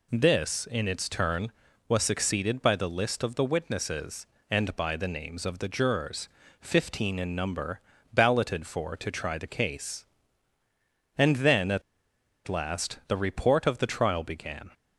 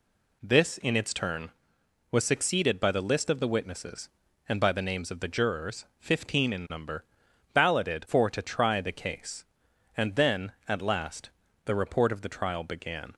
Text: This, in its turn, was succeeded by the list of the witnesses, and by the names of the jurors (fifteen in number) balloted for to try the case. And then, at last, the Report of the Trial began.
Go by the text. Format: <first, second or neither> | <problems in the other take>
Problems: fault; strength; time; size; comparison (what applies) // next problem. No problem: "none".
second | pauses between "at" and "last"; noticeable; at 11.8 s; 0.65 s long